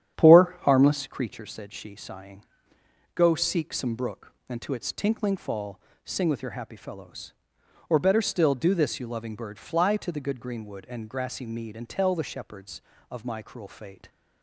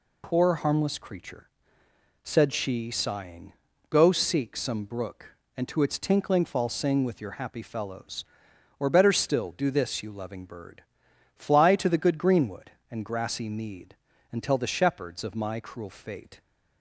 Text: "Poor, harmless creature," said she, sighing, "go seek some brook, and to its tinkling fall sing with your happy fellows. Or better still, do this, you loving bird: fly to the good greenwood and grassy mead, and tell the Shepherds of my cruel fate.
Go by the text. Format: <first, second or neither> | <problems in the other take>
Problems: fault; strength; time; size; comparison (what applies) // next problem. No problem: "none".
second | starts louder than the rest; strong; until 1.3 s; 9.5 dB // pauses between "fall" and "sing"; slight; at 5.7 s; 0.26 s long